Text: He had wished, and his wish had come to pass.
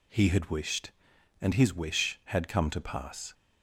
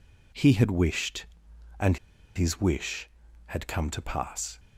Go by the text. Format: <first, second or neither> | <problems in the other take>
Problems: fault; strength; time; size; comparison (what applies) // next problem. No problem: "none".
first | pauses between "and" and "his"; at 1.9 s; 0.37 s long